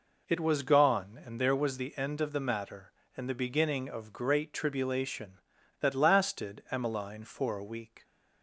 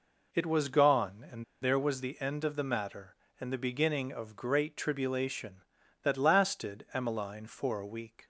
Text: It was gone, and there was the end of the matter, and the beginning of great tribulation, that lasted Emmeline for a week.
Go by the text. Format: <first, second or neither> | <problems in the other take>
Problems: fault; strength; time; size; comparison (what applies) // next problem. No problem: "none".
first | pauses between "and" and "there"; slight; at 1.4 s; 0.18 s long